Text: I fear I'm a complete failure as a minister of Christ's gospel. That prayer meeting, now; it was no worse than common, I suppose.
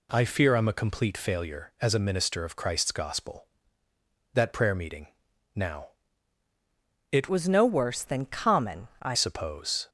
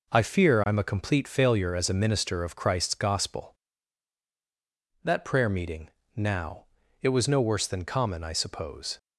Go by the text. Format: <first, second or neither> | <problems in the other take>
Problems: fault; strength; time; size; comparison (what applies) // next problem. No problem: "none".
second | changes voice from "was" to "I"; from 7.2 to 9.1 s; 1.9 s long